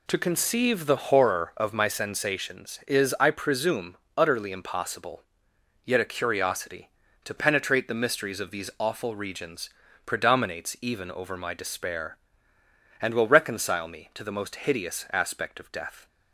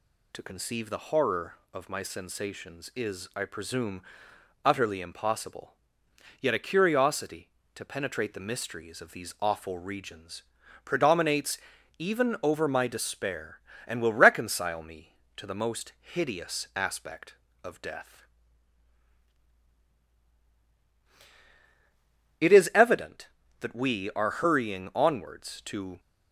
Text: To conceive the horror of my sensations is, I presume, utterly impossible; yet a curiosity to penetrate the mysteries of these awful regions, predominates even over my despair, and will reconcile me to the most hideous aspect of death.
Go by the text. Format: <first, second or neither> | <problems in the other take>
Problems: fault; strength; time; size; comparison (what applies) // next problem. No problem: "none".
first | pauses between "predominates" and "even"; at 11.5 s; 0.40 s long // goes on to say "It is evident that we are hurrying onwards to"; strong; from 22.3 s on; 3.6 s long